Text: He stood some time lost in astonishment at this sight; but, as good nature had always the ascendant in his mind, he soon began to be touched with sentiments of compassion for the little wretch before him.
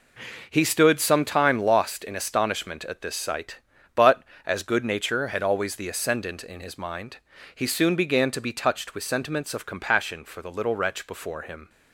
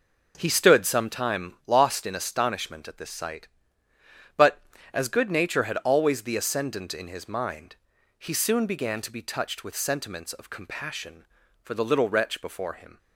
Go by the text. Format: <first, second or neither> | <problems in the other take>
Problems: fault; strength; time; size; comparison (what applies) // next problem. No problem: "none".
neither | none